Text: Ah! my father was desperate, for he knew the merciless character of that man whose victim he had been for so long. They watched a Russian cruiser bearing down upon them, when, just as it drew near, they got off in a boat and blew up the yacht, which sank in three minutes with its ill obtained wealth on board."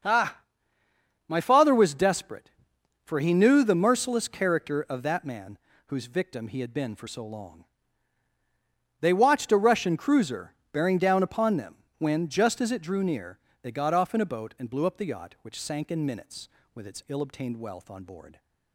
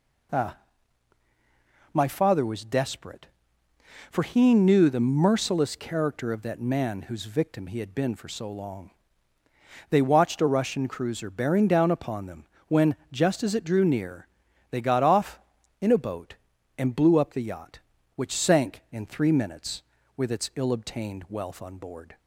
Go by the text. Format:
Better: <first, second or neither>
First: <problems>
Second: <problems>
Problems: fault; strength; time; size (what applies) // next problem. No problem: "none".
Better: second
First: starts louder than the rest; until 1.9 s; 6.5 dB // pauses between "man" and "whose"; slight; at 5.5 s; 0.28 s long // pauses between "cruiser" and "bearing"; slight; at 10.5 s; 0.20 s long // skips "three"; at 16.0 s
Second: none